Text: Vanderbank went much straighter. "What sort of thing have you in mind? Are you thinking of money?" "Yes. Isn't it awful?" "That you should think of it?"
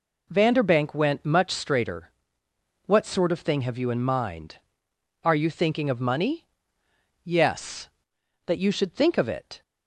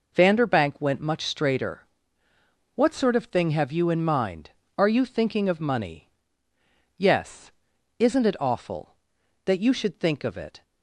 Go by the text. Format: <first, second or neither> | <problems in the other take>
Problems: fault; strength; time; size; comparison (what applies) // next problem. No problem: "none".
second | skips "Isn't it awful"; at 8.1 s